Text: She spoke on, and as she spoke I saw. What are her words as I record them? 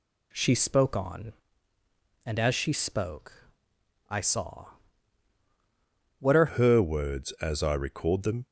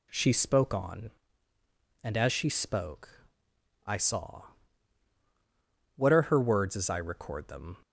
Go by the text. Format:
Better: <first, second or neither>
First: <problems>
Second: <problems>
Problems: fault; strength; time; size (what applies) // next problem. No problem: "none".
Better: second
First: pauses between "spoke" and "I"; noticeable; at 3.5 s; 0.58 s long // changes voice at "her"; from 6.4 s on; 2.0 s long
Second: pauses between "spoke" and "I"; noticeable; at 3.2 s; 0.58 s long